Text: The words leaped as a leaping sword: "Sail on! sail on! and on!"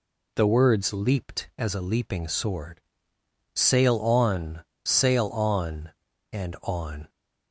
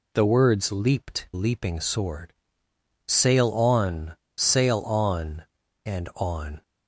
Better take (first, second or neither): first